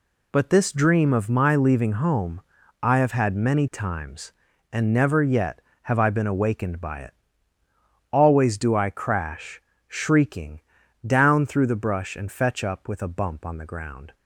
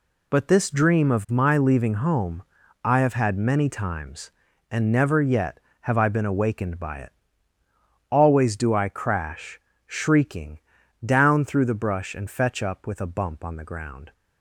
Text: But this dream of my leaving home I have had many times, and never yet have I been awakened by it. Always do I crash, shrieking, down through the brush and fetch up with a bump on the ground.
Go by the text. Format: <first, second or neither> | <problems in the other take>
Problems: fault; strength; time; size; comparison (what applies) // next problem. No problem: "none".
neither | pauses between "home" and "I"; the same in both